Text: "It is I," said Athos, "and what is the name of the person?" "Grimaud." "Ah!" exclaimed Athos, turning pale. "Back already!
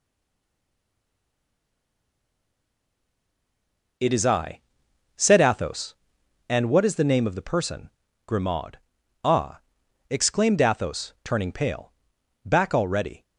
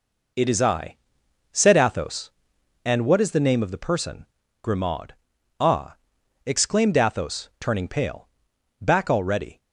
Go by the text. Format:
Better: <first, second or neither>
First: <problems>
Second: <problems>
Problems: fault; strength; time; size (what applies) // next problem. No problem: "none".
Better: second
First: stays silent before the first word; strong; until 3.9 s; 3.9 s long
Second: none